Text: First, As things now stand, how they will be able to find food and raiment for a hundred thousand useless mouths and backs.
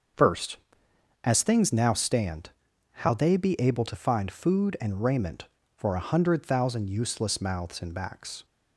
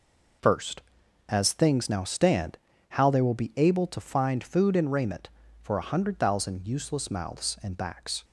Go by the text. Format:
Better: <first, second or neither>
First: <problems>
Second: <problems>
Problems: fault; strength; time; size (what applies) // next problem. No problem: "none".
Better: second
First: starts louder than the rest; until 1.8 s; 6.5 dB // skips "will"; at 3.3 s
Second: none